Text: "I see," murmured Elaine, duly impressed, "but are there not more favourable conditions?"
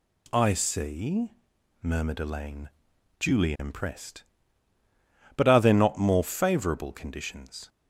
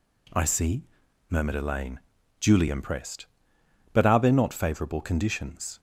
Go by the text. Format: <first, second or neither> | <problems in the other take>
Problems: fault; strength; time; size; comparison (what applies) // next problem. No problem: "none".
first | skips "more"; at 4.5 s